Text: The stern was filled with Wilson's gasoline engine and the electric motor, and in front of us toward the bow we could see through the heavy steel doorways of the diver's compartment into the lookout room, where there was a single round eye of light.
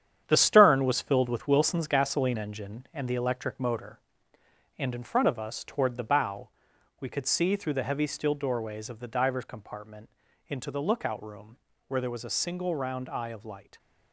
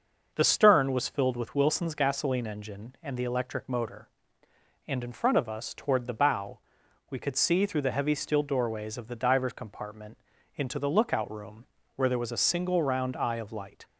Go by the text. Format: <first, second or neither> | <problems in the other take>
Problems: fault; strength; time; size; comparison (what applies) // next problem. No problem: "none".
second | gets quieter; strong; throughout; 8 dB // starts louder than the rest; strong; until 1.2 s; 9 dB; noticeable in the second // pauses between "bow" and "we"; noticeable; at 6.5 s; 0.50 s long; noticeable in the second // pauses between "compartment" and "into"; slight; at 10.1 s; 0.36 s long; slight in the second